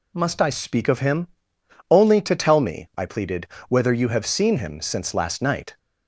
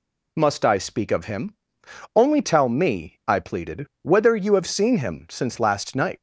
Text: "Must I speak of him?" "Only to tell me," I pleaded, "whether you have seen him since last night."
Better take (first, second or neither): first